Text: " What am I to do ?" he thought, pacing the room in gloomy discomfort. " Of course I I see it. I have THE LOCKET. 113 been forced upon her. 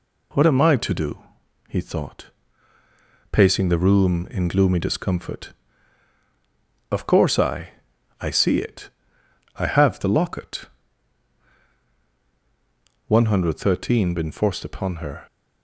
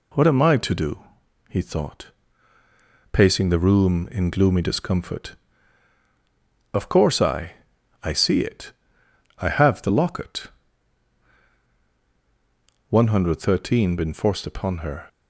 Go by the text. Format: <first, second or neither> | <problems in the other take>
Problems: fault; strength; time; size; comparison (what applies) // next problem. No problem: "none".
neither | pauses between "I" and "I"; noticeable; the same in both